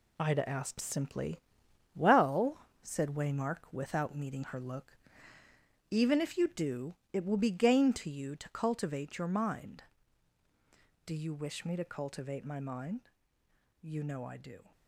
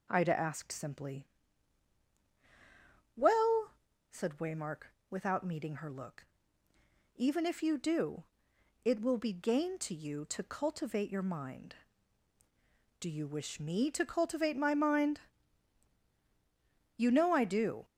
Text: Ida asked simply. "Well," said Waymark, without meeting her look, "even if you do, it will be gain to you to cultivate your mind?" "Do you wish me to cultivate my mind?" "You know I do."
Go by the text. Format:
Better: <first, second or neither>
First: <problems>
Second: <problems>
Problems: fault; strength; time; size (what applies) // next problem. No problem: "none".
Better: second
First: gets quieter; strong; throughout; 8.5 dB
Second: none